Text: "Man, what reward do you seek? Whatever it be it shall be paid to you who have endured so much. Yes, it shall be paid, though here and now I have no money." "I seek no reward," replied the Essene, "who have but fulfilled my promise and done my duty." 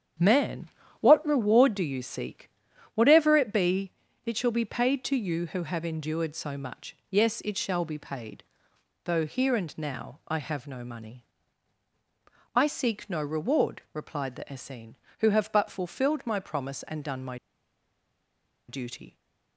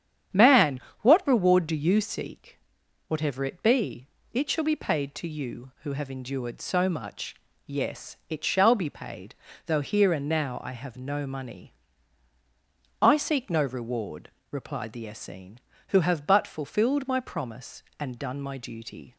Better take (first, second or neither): second